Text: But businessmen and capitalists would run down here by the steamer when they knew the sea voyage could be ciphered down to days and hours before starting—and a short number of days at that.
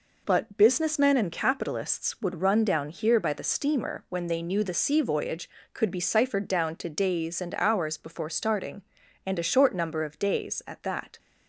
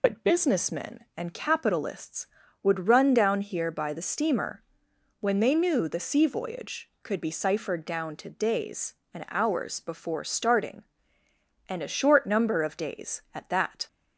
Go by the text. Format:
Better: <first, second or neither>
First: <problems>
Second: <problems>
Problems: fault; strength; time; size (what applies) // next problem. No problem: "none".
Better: first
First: none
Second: loses the start of "But"; at 0.0 s; 70 ms // pauses between "steamer" and "when"; noticeable; at 4.6 s; 0.60 s long